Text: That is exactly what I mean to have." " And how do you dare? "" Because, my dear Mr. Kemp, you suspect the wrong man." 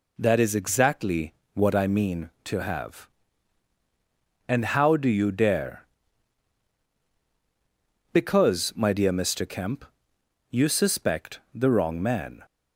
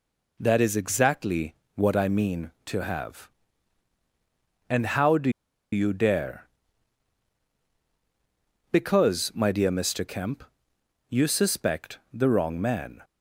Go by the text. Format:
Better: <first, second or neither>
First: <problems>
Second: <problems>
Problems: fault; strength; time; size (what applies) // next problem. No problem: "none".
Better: first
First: pauses between "exactly" and "what"; slight; at 1.3 s; 0.20 s long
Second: pauses between "exactly" and "what"; slight; at 1.5 s; 0.20 s long // pauses between "do" and "you"; at 5.2 s; 0.42 s long